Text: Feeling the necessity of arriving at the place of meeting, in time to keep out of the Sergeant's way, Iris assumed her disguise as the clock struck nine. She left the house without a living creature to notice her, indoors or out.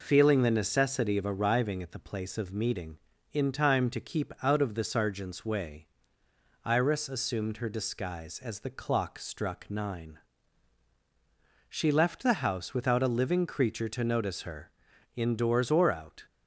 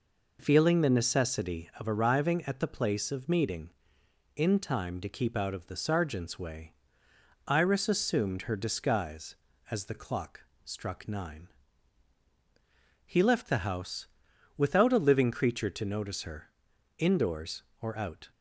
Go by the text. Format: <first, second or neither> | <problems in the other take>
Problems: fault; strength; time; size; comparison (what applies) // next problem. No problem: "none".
first | pauses between "clock" and "struck"; slight; at 10.4 s; 0.20 s long // says "He" for "She"; at 13.0 s // pauses between "house" and "without"; noticeable; at 14.0 s; 0.50 s long